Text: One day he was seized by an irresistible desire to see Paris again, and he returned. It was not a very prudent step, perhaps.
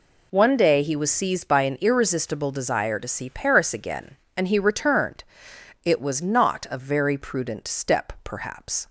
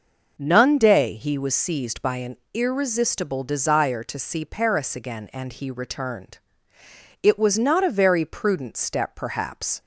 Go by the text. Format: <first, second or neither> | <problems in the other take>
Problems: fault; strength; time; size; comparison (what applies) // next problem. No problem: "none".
first | says "None" for "One"; at 0.3 s // pauses between "an" and "irresistible"; slight; at 2.3 s; 0.16 s long